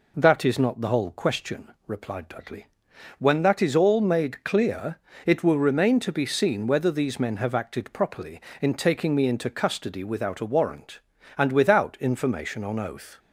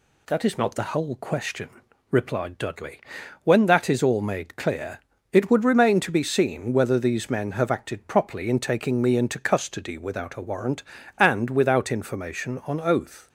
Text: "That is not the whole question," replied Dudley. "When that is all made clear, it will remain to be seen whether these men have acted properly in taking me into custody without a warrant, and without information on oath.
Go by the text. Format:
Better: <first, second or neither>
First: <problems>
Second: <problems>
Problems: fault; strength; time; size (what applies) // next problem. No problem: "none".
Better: first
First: none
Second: says "would" for "will"; at 5.5 s